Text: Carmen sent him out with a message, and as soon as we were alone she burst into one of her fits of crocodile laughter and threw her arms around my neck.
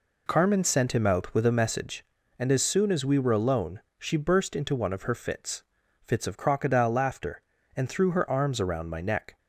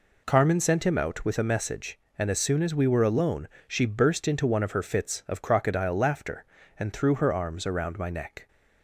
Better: second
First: pauses between "alone" and "she"; slight; at 3.7 s; 0.18 s long // says "fits" twice; at 6.0 s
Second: pauses between "alone" and "she"; slight; at 3.4 s; 0.20 s long

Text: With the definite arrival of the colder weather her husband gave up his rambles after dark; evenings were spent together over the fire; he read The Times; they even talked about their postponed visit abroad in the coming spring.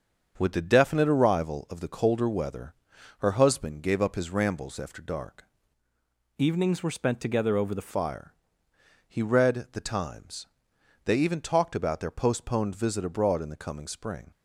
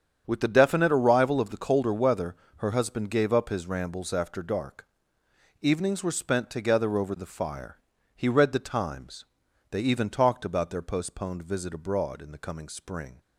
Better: second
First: starts louder than the rest; until 1.3 s; 7 dB // pauses between "weather" and "her"; noticeable; at 2.7 s; 0.46 s long // changes voice from "evenings" to "the"; from 6.3 to 7.8 s; 1.5 s long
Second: starts louder than the rest; strong; until 1.2 s; 8 dB // pauses between "weather" and "her"; slight; at 2.3 s; 0.22 s long

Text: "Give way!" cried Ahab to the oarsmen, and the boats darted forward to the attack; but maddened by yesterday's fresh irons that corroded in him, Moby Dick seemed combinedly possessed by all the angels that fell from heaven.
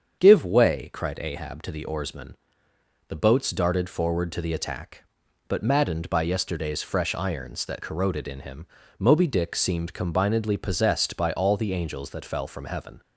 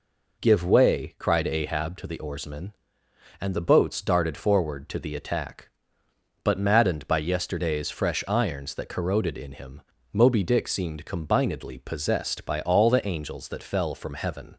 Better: second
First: starts louder than the rest; strong; until 1.2 s; 7 dB // skips "and"; at 2.7 s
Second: none

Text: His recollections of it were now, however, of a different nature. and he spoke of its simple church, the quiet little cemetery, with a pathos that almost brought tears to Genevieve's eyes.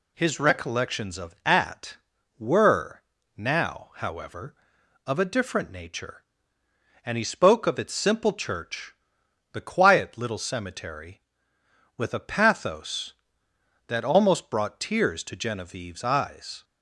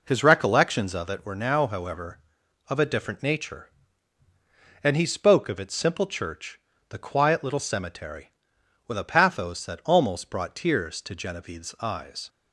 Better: second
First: says "at" for "it"; at 1.4 s // pauses between "were" and "now"; slight; at 3.0 s; 0.34 s long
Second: none

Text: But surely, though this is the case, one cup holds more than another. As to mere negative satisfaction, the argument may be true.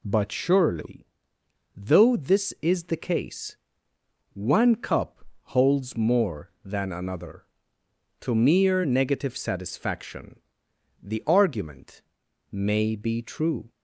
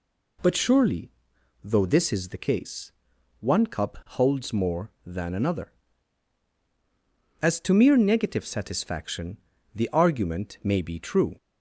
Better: second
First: pauses between "cup" and "holds"; slight; at 5.2 s; 0.18 s long // skips "As"; at 7.8 s // pauses between "argument" and "may"; noticeable; at 12.0 s; 0.50 s long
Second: none

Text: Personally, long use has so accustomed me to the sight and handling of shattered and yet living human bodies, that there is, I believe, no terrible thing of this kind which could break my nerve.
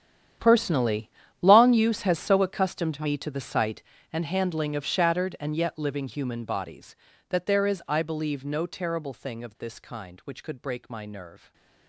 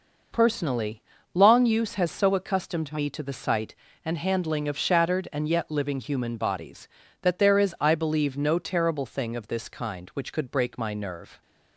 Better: second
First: gets quieter; strong; throughout; 16.5 dB // stays silent after the last word; slight; from 11.3 s on; 0.5 s long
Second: none

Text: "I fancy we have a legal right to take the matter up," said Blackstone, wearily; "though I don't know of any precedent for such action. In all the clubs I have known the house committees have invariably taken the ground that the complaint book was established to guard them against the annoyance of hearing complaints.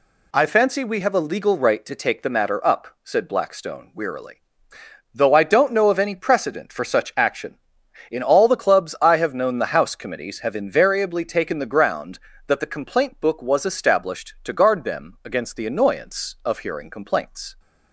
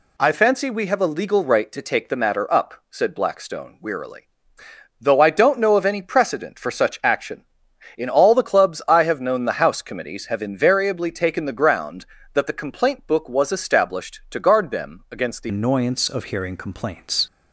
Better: first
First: none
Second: changes voice at "annoyance"; from 15.4 s on; 1.8 s long

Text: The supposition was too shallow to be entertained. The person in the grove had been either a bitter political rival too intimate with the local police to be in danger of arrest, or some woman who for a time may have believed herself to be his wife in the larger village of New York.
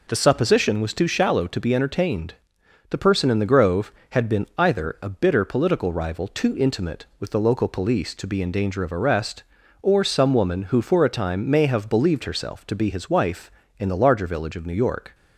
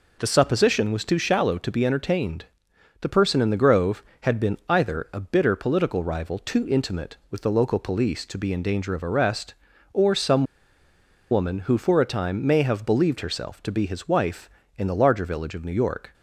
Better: first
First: none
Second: pauses between "some" and "woman"; noticeable; at 10.4 s; 0.87 s long

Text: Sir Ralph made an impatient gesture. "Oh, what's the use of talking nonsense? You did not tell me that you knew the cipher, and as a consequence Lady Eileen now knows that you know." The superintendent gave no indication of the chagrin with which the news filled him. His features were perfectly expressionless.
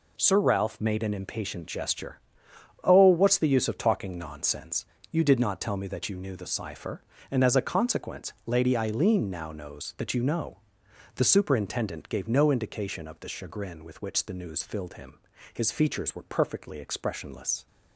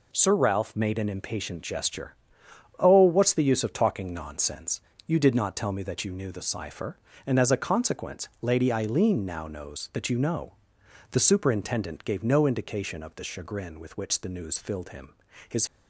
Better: first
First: none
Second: stops before "features were perfectly expressionless"; at 15.6 s

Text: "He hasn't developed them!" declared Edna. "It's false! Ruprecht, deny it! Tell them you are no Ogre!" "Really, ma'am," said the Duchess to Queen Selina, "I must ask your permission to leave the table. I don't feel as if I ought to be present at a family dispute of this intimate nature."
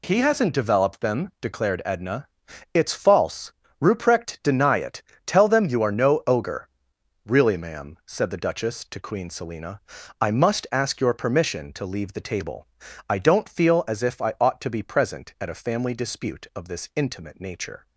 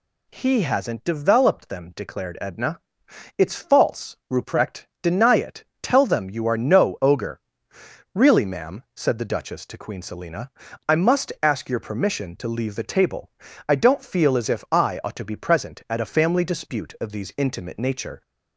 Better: first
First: none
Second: says "these" for "this"; at 17.1 s

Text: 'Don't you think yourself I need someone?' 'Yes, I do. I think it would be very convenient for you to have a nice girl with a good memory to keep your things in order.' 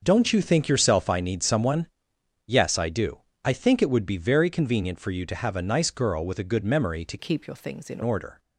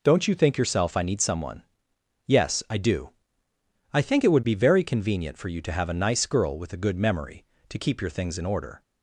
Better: second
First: starts louder than the rest; until 1.0 s; 6.5 dB // changes voice from "keep" to "in"; from 7.1 to 8.0 s; 0.9 s long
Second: none

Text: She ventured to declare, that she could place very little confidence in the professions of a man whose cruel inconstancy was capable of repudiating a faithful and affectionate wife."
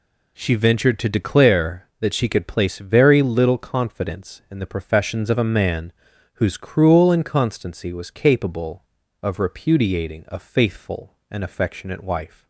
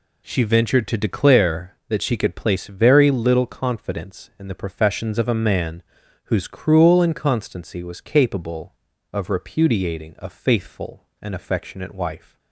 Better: neither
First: pauses between "man" and "whose"; at 5.9 s; 0.40 s long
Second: pauses between "man" and "whose"; at 5.8 s; 0.40 s long

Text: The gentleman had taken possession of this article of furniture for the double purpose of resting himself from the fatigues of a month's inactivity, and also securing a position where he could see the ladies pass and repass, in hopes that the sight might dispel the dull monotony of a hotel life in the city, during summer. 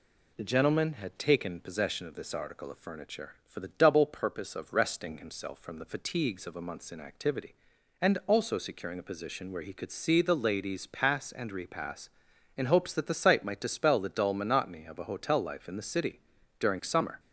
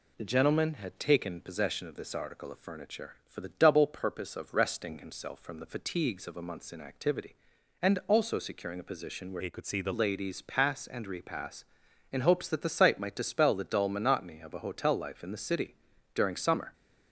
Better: first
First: none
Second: changes voice from "he" to "the"; from 9.3 to 9.9 s; 0.6 s long

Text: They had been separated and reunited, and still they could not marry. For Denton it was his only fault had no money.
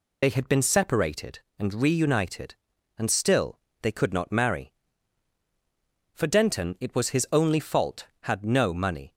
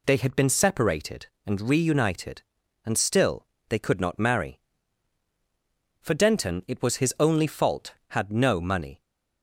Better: second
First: loses the start of "They"; at 0.2 s; 50 ms // pauses between "still" and "they"; slight; at 3.5 s; 0.22 s long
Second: pauses between "still" and "they"; slight; at 3.4 s; 0.22 s long

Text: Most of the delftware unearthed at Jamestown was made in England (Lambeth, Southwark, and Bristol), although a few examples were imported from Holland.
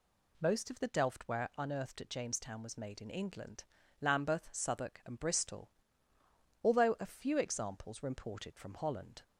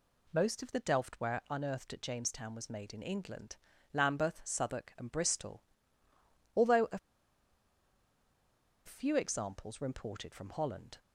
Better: first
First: none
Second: pauses between "a" and "few"; strong; at 6.9 s; 1.8 s long

